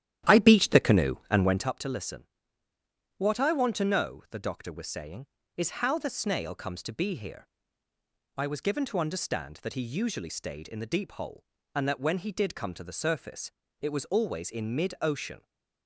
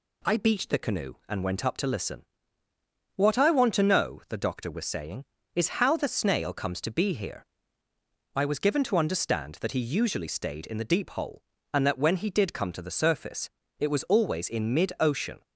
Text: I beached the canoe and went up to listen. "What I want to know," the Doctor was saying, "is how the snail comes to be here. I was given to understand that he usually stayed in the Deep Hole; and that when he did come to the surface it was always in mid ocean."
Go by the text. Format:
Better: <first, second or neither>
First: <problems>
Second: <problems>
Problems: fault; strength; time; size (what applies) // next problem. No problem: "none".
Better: second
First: starts louder than the rest; strong; until 1.7 s; 12 dB // pauses between "surface" and "it"; slight; at 13.5 s; 0.32 s long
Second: pauses between "surface" and "it"; slight; at 13.4 s; 0.32 s long